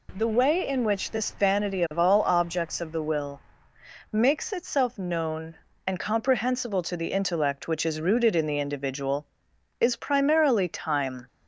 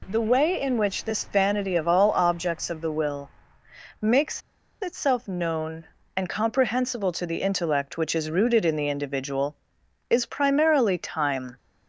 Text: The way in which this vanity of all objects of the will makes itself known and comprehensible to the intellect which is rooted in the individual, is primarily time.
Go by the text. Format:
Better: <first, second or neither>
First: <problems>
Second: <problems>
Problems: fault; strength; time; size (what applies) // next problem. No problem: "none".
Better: first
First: pauses between "will" and "makes"; noticeable; at 3.4 s; 0.72 s long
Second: pauses between "will" and "makes"; noticeable; at 3.2 s; 0.72 s long // pauses between "makes" and "itself"; at 4.4 s; 0.41 s long